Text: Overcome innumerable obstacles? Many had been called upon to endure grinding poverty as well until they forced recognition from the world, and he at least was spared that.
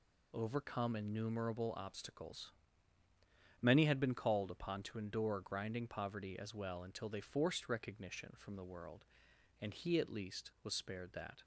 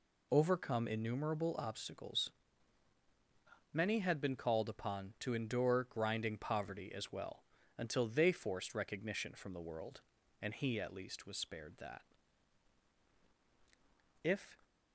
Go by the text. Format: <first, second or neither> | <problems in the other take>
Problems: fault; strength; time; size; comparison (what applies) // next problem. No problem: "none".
first | pauses between "well" and "until"; slight; at 7.4 s; 0.34 s long // goes on to say "If"; slight; from 14.2 s on; 0.34 s long